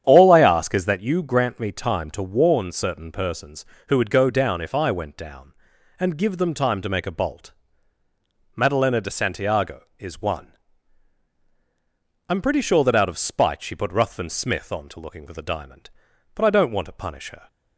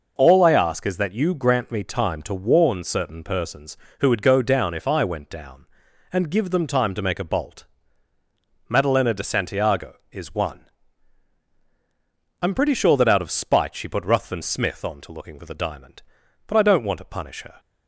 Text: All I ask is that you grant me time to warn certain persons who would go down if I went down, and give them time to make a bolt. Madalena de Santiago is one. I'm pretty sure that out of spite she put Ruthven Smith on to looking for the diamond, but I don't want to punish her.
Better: second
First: starts louder than the rest; strong; until 1.0 s; 9 dB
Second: none

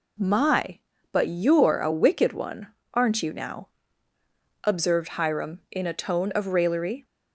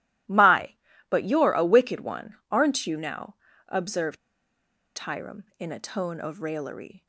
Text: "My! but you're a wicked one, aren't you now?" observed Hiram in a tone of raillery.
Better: first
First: none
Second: starts louder than the rest; strong; until 1.6 s; 15.5 dB // pauses between "observed" and "Hiram"; noticeable; at 4.1 s; 0.80 s long

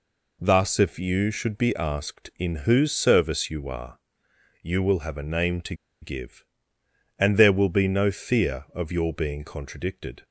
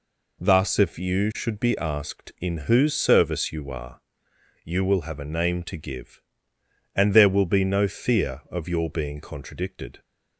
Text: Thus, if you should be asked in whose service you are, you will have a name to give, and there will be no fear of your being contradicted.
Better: second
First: pauses between "to" and "give"; slight; at 5.7 s; 0.27 s long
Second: none

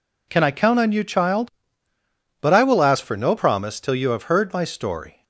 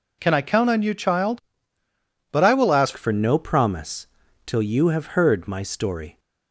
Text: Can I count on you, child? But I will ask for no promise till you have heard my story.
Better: first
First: none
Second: changes voice at "for"; from 2.9 s on; 3.2 s long // pauses between "promise" and "till"; at 4.0 s; 0.38 s long

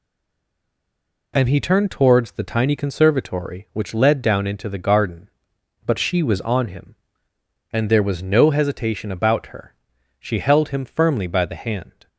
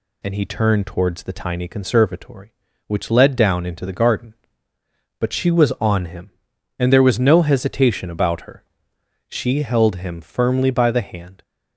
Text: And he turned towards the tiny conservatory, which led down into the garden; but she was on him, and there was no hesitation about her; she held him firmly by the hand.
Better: second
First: stays silent before the first word; noticeable; until 1.3 s; 1.3 s long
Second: none

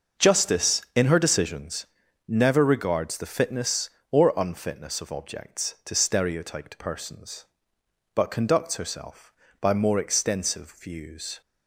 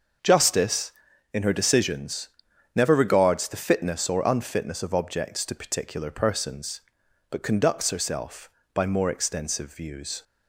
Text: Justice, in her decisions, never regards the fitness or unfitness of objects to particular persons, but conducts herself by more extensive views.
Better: second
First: starts louder than the rest; noticeable; until 1.3 s; 6 dB // says "stereotyped" for "particular"; at 5.9 s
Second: starts louder than the rest; until 1.6 s; 6 dB

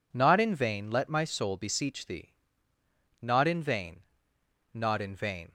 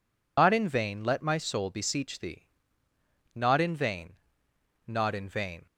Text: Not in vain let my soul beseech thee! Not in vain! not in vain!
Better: first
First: none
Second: loses the start of "Not"; at 0.3 s; 120 ms

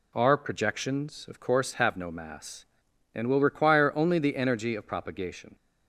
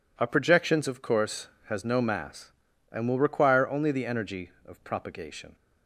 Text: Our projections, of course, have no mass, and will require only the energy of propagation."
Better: first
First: none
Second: says "has" for "have"; at 1.6 s

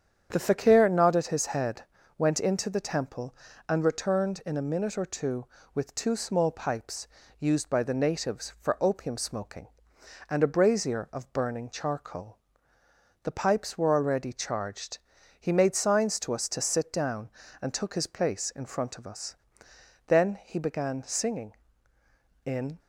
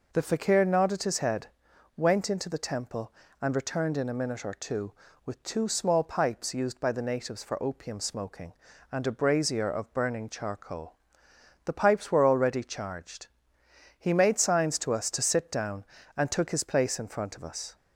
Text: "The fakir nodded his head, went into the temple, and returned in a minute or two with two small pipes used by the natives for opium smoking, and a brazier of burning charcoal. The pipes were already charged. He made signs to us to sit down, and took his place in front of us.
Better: second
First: starts louder than the rest; strong; until 1.3 s; 8 dB // pauses between "pipes" and "used"; slight; at 7.0 s; 0.34 s long // goes on to say "Then he began singing in"; strong; from 20.0 s on; 2.7 s long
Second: none

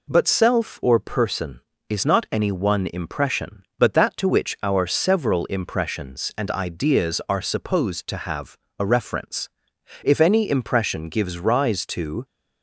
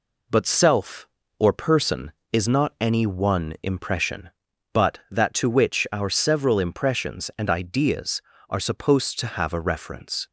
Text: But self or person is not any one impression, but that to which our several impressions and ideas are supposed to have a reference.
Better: second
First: pauses between "have" and "a"; slight; at 8.5 s; 0.22 s long // goes on to say "If any impression gives rise to"; strong; from 10.0 s on; 2.2 s long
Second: none

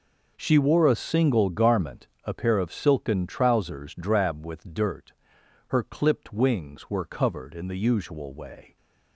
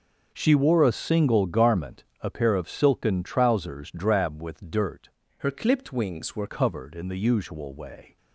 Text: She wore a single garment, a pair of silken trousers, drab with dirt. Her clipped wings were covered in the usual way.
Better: first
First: none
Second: changes voice from "Her" to "were"; from 5.3 to 6.4 s; 1.1 s long

